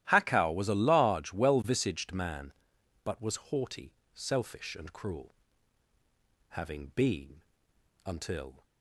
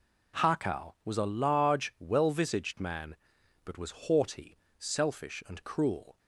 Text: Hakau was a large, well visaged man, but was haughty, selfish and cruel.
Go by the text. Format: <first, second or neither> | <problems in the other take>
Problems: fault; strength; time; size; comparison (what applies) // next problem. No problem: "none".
second | starts louder than the rest; strong; until 1.1 s; 13 dB // pauses between "was" and "haughty"; slight; at 3.3 s; 0.16 s long // goes on to say "Having been until"; strong; from 6.5 s on; 2.1 s long